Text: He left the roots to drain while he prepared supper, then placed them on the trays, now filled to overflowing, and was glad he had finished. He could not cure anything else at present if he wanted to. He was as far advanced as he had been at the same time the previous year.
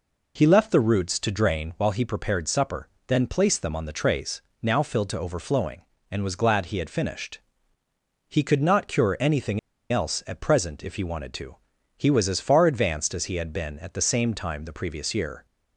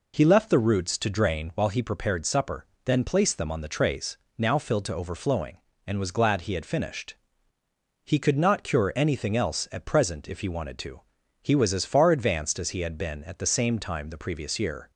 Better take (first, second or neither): second